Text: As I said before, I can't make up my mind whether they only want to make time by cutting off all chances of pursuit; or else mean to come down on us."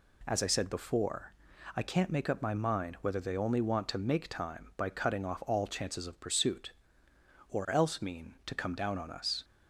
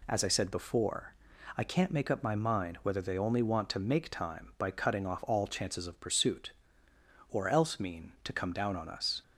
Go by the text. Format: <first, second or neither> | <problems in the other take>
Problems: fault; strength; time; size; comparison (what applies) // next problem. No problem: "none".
neither | none